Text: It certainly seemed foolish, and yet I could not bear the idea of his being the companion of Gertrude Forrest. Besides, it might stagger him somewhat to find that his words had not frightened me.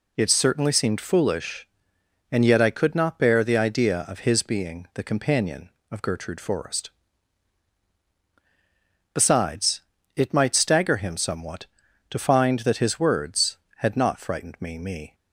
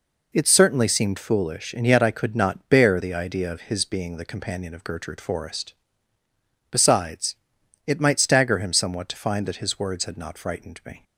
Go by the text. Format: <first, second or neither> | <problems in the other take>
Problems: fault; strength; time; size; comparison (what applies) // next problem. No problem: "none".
second | says "me" twice; at 14.7 s